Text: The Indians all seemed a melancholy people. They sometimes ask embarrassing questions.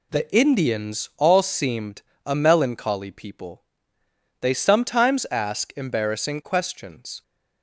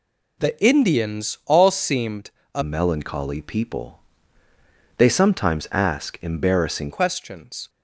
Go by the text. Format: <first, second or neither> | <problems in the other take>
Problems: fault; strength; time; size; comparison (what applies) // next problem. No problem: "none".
first | pauses between "seemed" and "a"; slight; at 2.3 s; 0.24 s long; slight in the first // changes voice from "melancholy" to "embarrassing"; from 2.6 to 6.9 s; 4.3 s long